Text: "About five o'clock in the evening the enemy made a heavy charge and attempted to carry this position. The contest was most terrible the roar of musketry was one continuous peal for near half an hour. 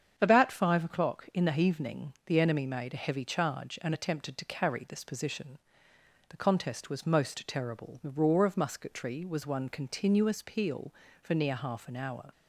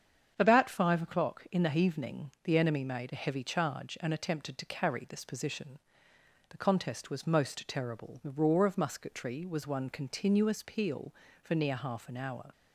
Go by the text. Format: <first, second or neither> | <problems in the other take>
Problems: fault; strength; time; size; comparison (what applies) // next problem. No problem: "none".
neither | starts louder than the rest; strong; the same in both